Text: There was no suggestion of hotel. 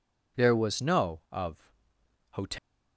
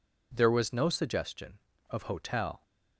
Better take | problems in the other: second | skips "suggestion"; at 1.2 s // pauses between "of" and "hotel"; noticeable; at 1.7 s; 0.60 s long

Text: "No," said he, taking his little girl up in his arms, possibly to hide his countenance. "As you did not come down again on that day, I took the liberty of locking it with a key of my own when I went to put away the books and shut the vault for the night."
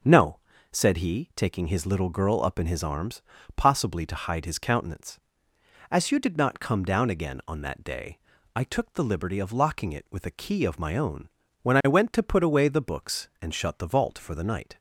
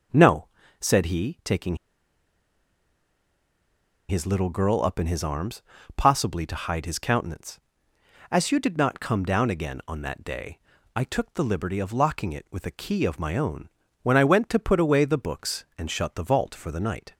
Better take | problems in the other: first | starts louder than the rest; until 1.5 s; 6 dB; also in the first // pauses between "taking" and "his"; strong; at 1.7 s; 2.3 s long // pauses between "own" and "when"; slight; at 13.6 s; 0.32 s long; slight in the first

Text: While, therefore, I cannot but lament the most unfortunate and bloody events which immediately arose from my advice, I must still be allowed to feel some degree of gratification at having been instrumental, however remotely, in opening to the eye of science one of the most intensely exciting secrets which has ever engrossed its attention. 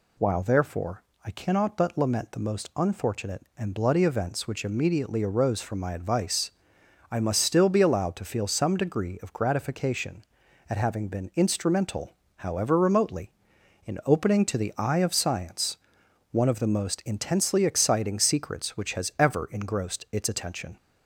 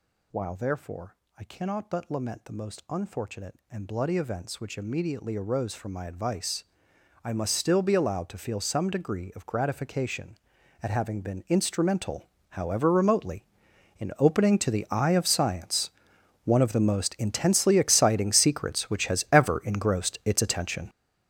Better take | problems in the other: first | gets louder; strong; throughout; 12.5 dB // pauses between "science" and "one"; noticeable; at 15.8 s; 0.56 s long; noticeable in the first

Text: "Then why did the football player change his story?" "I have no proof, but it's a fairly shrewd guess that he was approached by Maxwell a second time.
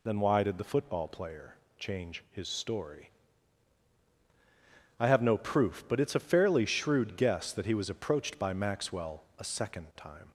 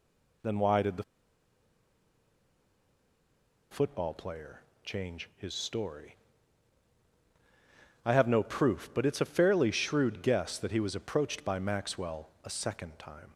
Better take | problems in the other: first | pauses between "the" and "football"; strong; at 1.0 s; 2.6 s long // pauses between "player" and "change"; slight; at 4.6 s; 0.20 s long; slight in the first

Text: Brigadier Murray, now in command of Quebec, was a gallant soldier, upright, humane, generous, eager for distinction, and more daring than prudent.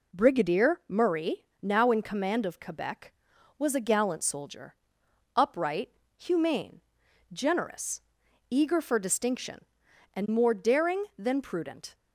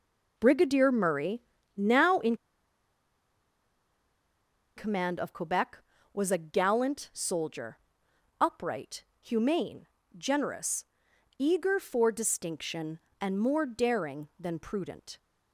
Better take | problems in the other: first | pauses between "in" and "command"; strong; at 2.3 s; 2.4 s long

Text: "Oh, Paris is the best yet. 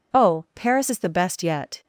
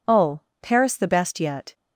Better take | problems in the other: first | skips "is"; at 0.9 s

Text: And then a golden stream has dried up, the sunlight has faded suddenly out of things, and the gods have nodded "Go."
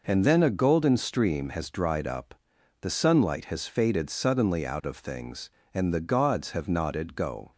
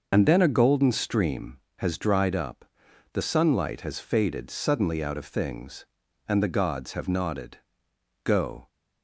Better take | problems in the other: first | loses the start of "And"; at 0.1 s; 40 ms // pauses between "nodded" and "Go"; noticeable; at 7.5 s; 0.64 s long

